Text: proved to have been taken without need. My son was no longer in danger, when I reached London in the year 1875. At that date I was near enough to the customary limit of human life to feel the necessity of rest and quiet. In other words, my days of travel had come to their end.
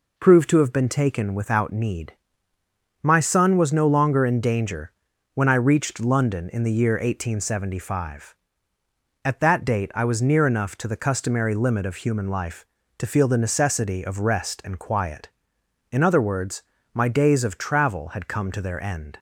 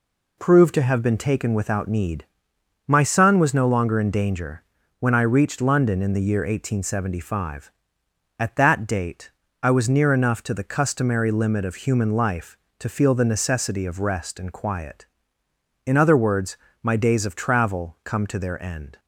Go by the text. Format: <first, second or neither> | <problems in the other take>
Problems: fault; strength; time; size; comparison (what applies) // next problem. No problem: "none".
first | pauses between "date" and "I"; slight; at 9.3 s; 0.30 s long // skips "had"; at 18.0 s